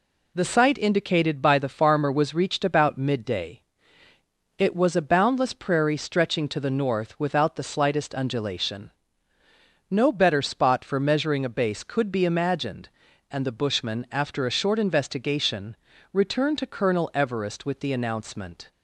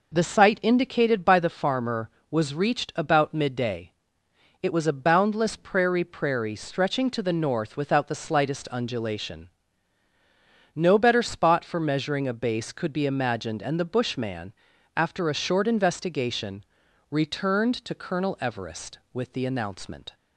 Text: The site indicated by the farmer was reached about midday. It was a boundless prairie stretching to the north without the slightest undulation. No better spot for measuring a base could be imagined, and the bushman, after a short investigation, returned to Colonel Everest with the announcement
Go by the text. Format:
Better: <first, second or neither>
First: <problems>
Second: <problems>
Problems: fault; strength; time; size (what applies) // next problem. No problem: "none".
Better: first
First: none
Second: says "prairie" twice; at 6.0 s